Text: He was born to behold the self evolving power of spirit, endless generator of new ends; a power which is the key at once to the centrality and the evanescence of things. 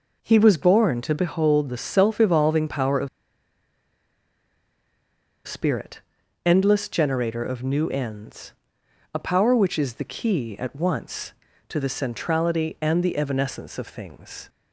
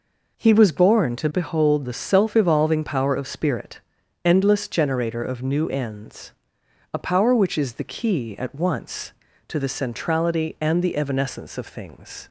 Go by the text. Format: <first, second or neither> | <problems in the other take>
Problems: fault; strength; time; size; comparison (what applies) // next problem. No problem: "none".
second | pauses between "of" and "spirit"; strong; at 3.0 s; 2.3 s long